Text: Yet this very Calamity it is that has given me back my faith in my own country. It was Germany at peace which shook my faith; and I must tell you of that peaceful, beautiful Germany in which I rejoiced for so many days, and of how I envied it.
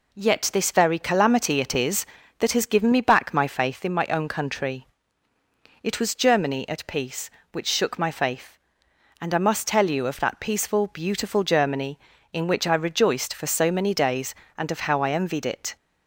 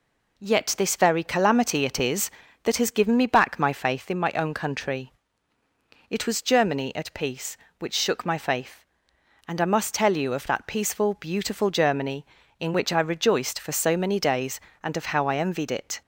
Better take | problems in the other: neither | none

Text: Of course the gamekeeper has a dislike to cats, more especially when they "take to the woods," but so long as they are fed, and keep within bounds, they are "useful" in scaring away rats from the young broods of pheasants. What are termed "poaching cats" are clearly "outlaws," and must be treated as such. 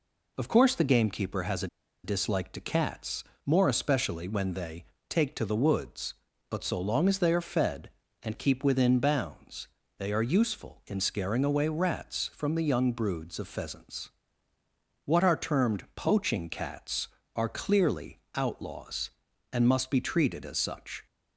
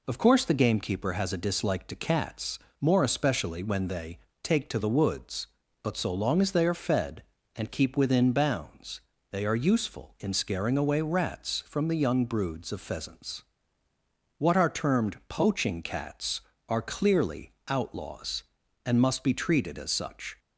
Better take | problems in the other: second | pauses between "a" and "dislike"; at 1.6 s; 0.37 s long // pauses between "they" and "take"; slight; at 4.8 s; 0.26 s long; slight in the second // pauses between "clearly" and "outlaws"; slight; at 18.1 s; 0.16 s long; slight in the second

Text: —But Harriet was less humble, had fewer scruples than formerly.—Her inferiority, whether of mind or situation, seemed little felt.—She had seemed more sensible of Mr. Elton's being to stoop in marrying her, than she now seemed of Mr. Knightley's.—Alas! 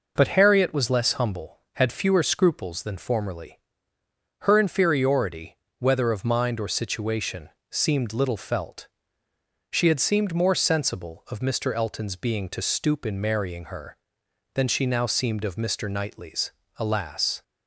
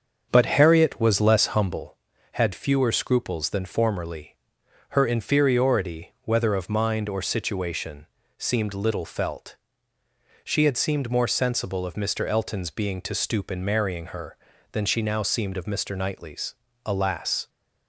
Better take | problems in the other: first | starts louder than the rest; until 1.8 s; 7 dB

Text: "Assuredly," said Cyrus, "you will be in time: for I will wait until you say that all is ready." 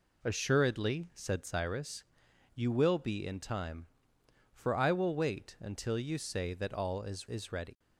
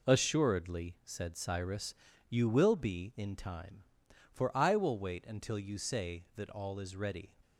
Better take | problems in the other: second | says "is" twice; at 7.2 s

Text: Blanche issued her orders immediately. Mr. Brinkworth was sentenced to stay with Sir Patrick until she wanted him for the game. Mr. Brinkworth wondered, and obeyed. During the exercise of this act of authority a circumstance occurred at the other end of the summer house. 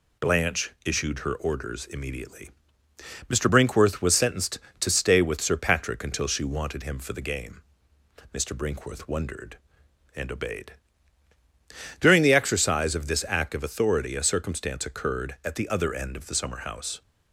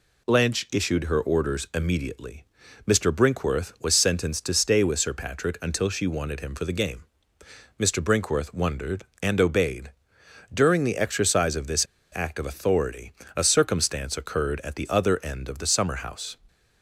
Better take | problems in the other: first | pauses between "this" and "act"; slight; at 11.8 s; 0.29 s long // pauses between "authority" and "a"; slight; at 13.1 s; 0.24 s long

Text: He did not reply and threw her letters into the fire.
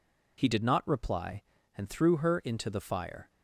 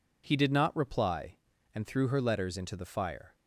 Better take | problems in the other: second | skips "letters"; at 2.3 s

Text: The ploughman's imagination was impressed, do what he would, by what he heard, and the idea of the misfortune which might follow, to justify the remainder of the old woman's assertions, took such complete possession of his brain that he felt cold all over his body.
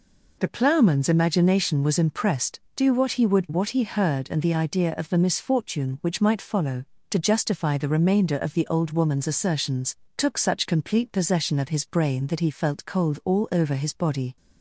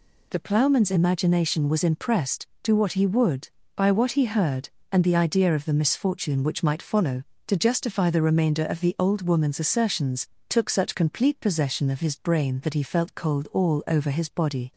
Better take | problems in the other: second | skips "by"; at 3.4 s

